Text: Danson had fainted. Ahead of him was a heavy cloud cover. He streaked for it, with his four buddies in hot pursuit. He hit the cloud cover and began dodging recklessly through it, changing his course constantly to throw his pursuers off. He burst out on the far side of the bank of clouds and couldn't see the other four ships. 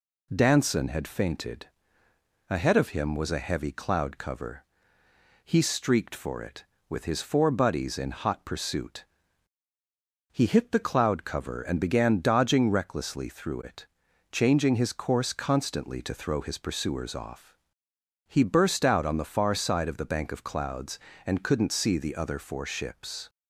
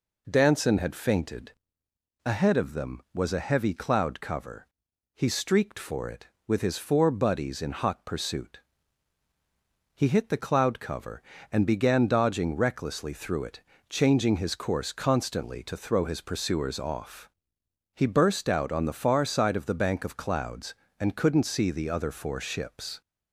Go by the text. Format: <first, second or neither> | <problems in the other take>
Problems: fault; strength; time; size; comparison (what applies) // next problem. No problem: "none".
first | says "them" for "him"; at 2.7 s